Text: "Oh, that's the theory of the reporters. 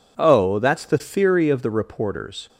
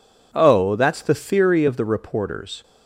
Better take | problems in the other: neither | none

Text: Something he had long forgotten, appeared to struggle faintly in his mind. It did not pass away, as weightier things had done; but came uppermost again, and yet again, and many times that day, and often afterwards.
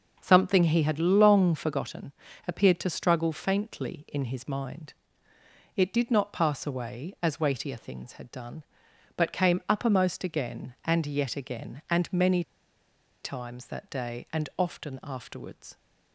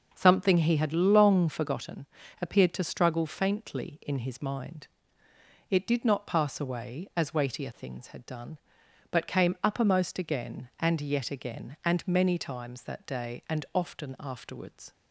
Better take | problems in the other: second | pauses between "many" and "times"; noticeable; at 12.4 s; 0.81 s long

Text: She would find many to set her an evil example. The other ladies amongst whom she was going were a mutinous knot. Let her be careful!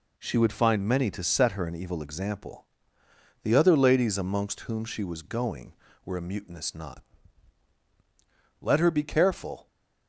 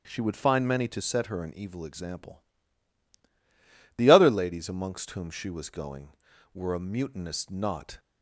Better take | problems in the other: first | starts louder than the rest; strong; until 1.0 s; 9 dB // stops before "Let her be careful"; at 7.9 s

